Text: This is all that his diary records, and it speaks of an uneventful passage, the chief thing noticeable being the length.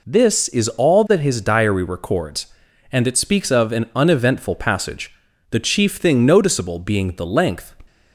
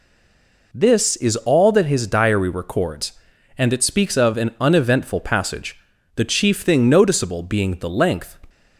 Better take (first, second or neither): first